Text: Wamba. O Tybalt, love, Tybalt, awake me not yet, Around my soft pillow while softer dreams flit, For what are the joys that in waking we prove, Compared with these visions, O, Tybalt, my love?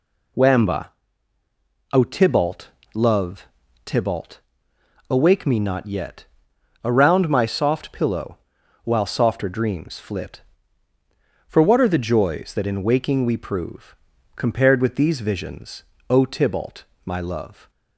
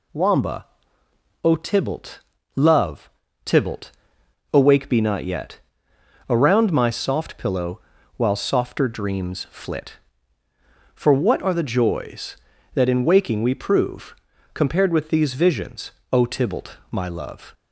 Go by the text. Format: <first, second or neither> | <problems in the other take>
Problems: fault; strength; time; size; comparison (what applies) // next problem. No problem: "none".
first | says "be" for "me"; at 4.8 s // pauses between "pillow" and "while"; at 7.7 s; 0.38 s long; noticeable in the first